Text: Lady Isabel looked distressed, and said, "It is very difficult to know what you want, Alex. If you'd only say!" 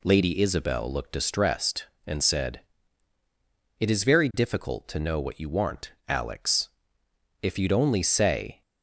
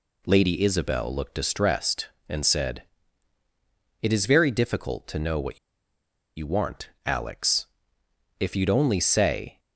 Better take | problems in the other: first | pauses between "what" and "you"; noticeable; at 5.5 s; 0.78 s long

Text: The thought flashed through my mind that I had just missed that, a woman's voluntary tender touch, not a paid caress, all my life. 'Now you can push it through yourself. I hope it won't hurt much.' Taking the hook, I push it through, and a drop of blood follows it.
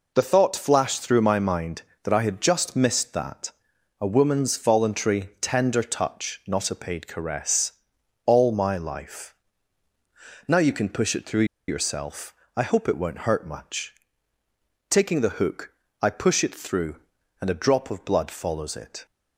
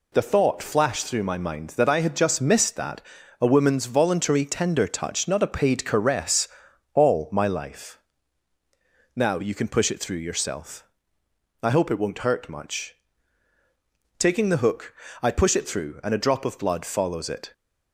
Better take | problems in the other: second | pauses between "through" and "yourself"; slight; at 11.4 s; 0.22 s long

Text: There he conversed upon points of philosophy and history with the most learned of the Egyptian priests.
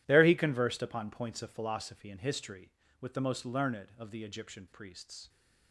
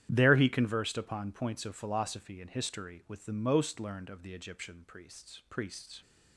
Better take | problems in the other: first | starts louder than the rest; strong; until 1.1 s; 11 dB // says "priests" twice; at 5.5 s

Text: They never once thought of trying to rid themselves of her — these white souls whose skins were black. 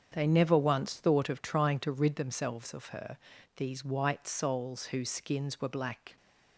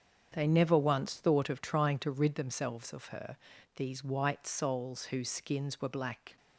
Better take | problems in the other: neither | starts louder than the rest; strong; the same in both

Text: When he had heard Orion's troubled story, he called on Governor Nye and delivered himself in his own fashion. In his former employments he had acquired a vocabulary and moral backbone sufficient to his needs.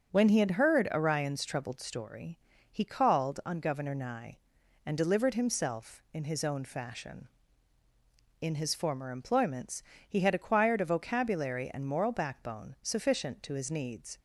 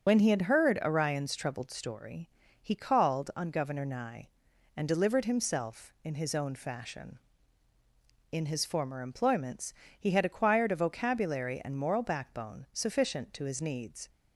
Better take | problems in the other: first | loses the start of "When"; at 0.0 s; 55 ms // starts louder than the rest; until 1.0 s; 7 dB; also in the first // pauses between "employments" and "he"; slight; at 9.7 s; 0.26 s long; slight in the first

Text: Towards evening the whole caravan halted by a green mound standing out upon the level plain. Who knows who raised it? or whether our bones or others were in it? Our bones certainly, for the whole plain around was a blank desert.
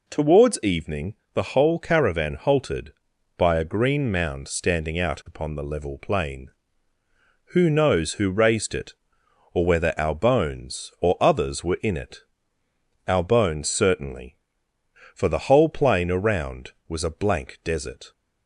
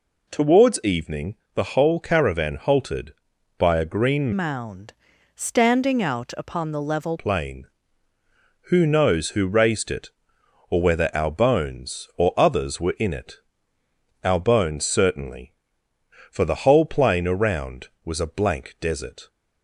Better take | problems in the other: first | pauses between "evening" and "the"; slight; at 1.3 s; 0.18 s long; slight in the first // changes voice from "mound" to "level"; from 4.3 to 7.1 s; 2.8 s long // pauses between "mound" and "standing"; at 4.9 s; 0.42 s long

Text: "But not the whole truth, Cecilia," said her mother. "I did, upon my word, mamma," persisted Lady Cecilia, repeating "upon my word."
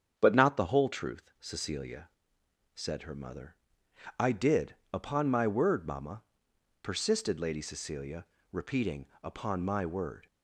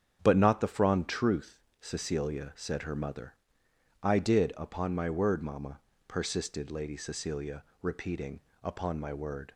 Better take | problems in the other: first | starts louder than the rest; strong; until 1.2 s; 8.5 dB; strong in the first // says "frond" for "whole"; at 0.6 s // pauses between "repeating" and "upon"; slight; at 8.4 s; 0.20 s long; slight in the first

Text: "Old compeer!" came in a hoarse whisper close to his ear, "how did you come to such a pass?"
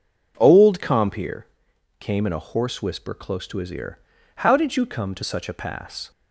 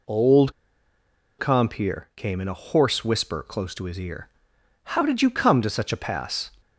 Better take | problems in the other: first | pauses between "Old" and "compeer"; noticeable; at 0.5 s; 0.86 s long

